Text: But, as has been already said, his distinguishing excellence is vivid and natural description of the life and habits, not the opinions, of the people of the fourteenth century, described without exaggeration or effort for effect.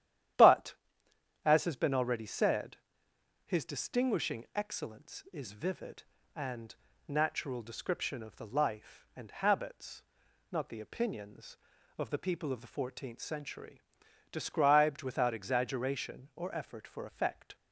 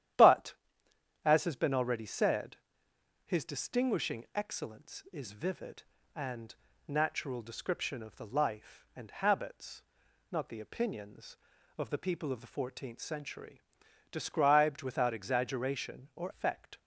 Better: first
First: starts louder than the rest; strong; until 2.0 s; 11 dB // pauses between "and" and "natural"; slight; at 6.7 s; 0.32 s long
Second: starts louder than the rest; strong; until 1.8 s; 11 dB // pauses between "and" and "natural"; slight; at 6.5 s; 0.32 s long // skips "effort for"; at 16.3 s

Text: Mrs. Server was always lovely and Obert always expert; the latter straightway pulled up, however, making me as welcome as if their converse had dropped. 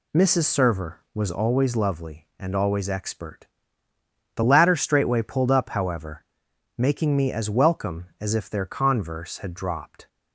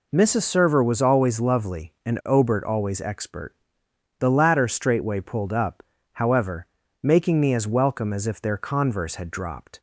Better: second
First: skips "Obert"; at 2.5 s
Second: none

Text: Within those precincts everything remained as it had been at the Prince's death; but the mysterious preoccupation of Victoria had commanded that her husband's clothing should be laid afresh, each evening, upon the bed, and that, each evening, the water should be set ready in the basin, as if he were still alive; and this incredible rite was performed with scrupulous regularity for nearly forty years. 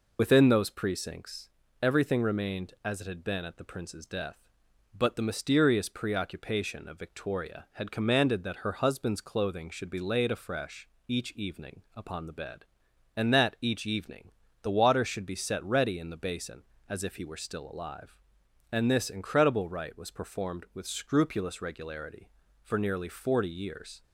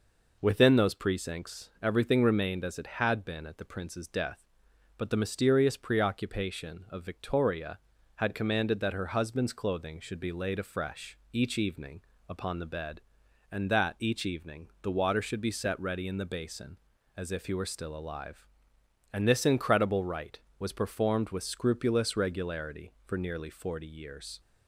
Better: second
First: loses the start of "Within"; at 0.1 s; 55 ms // pauses between "precincts" and "everything"; slight; at 1.4 s; 0.34 s long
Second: none

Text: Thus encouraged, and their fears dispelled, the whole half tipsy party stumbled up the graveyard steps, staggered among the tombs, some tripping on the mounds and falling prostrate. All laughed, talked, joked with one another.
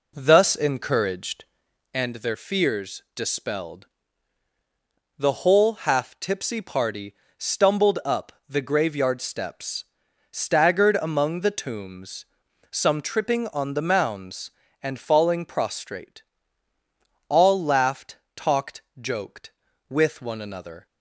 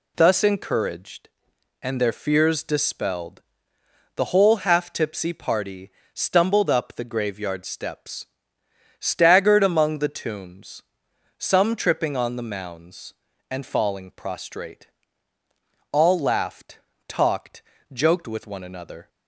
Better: second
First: starts louder than the rest; until 1.9 s; 3.5 dB // pauses between "party" and "stumbled"; slight; at 7.1 s; 0.22 s long // pauses between "up" and "the"; slight; at 8.3 s; 0.16 s long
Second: pauses between "party" and "stumbled"; slight; at 5.8 s; 0.24 s long

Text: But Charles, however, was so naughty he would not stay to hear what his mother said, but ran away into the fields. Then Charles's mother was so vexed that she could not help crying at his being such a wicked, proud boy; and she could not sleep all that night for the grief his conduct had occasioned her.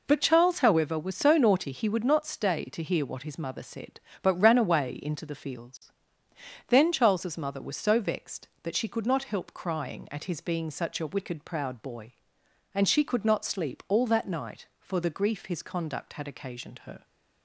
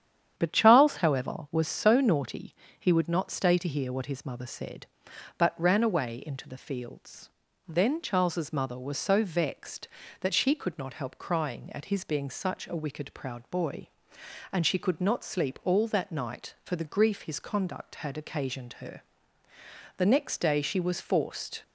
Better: first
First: none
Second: starts louder than the rest; strong; until 1.3 s; 9.5 dB // pauses between "naughty" and "he"; slight; at 2.5 s; 0.24 s long // goes on to say "The next day she was forced"; from 19.9 s on; 1.6 s long

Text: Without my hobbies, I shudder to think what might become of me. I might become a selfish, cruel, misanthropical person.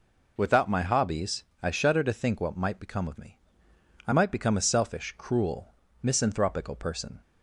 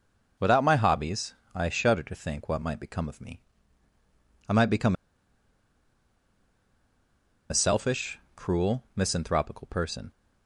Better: first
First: none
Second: pauses between "become" and "a"; strong; at 4.9 s; 2.5 s long

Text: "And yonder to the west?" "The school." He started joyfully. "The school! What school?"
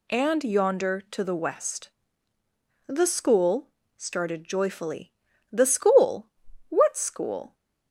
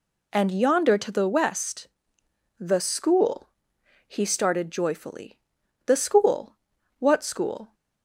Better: second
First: skips "He"; at 3.8 s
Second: none

